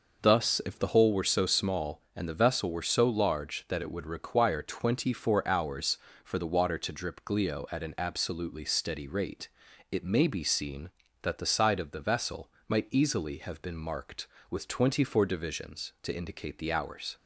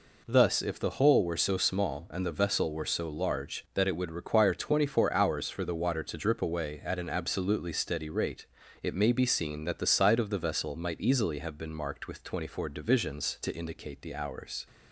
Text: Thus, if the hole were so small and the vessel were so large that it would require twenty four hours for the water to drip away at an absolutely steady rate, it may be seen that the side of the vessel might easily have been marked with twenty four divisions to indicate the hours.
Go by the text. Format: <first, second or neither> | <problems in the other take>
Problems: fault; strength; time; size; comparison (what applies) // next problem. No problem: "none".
second | says "glio" for "away"; at 7.2 s // pauses between "vessel" and "might"; slight; at 12.4 s; 0.18 s long